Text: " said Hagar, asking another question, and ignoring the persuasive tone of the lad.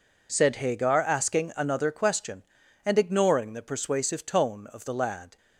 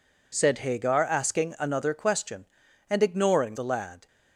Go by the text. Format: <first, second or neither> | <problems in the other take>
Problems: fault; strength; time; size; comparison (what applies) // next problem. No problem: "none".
first | skips "the persuasive tone of"; at 3.5 s